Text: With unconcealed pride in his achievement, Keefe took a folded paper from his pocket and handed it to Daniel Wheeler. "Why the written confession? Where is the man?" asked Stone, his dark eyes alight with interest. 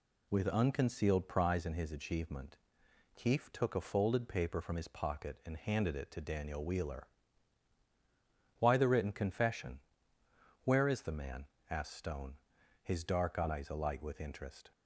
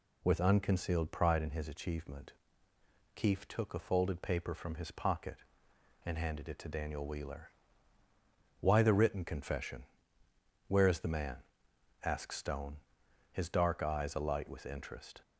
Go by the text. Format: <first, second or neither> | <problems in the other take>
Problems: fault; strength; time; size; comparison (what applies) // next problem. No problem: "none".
second | says "prize" for "pride"; at 1.2 s